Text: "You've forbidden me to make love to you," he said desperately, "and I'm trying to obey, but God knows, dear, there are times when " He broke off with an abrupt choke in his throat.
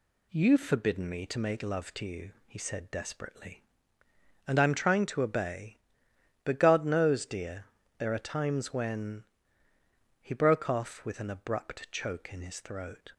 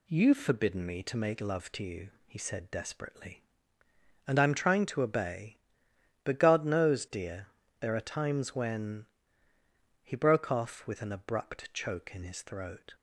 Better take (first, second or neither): neither